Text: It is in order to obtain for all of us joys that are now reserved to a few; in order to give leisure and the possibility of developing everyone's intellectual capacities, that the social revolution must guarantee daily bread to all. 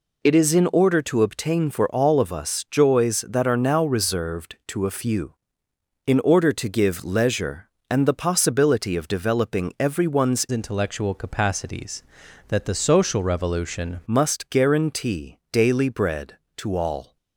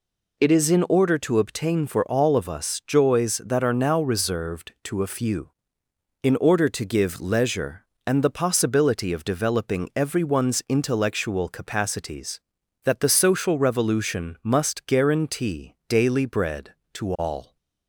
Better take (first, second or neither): second